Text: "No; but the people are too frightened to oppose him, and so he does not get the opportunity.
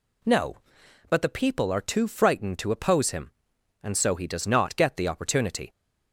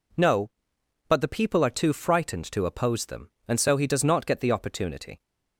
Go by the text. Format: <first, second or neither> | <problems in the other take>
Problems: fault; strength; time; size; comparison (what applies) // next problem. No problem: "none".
first | says "them" for "him"; at 3.0 s